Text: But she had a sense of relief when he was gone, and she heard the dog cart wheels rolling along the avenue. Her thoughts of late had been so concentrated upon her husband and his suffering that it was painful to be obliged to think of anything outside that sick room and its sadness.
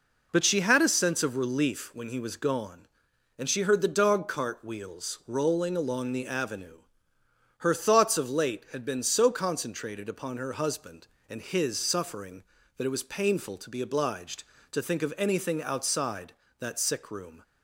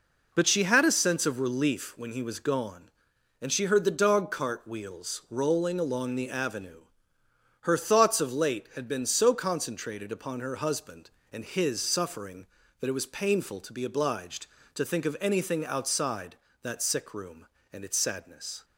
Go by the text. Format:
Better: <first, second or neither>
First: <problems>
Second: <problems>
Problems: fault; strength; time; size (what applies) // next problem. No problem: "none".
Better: second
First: stops before "and its sadness"; at 17.4 s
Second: none